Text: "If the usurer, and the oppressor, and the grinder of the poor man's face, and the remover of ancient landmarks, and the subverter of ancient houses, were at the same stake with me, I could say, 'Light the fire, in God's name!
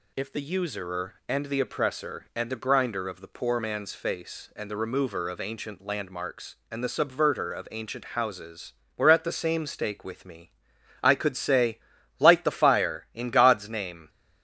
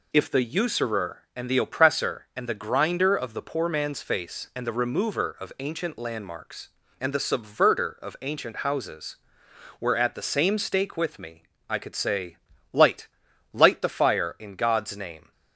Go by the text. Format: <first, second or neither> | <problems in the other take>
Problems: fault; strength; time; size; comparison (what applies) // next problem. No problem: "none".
first | says "Light" twice; at 13.5 s